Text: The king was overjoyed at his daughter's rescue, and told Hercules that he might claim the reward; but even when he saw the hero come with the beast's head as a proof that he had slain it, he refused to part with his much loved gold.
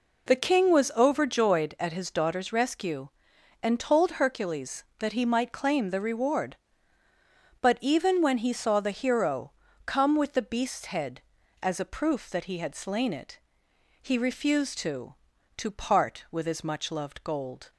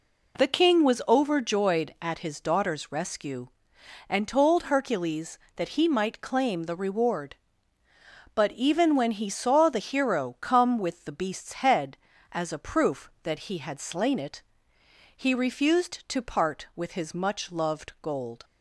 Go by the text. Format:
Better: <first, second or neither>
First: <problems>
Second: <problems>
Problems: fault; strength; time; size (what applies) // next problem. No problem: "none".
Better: second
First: pauses between "hero" and "come"; slight; at 9.5 s; 0.32 s long // says "to" twice; at 15.5 s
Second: none